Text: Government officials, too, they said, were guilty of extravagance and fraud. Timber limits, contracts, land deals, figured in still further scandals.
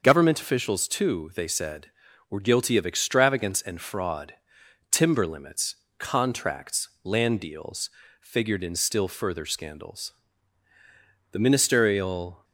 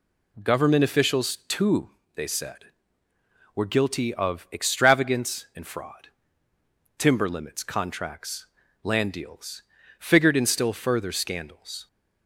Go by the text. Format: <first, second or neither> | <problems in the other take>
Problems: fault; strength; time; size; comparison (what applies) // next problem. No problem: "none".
second | starts louder than the rest; noticeable; until 1.0 s; 6 dB // goes on to say "The ministerial"; noticeable; from 11.3 s on; 1.1 s long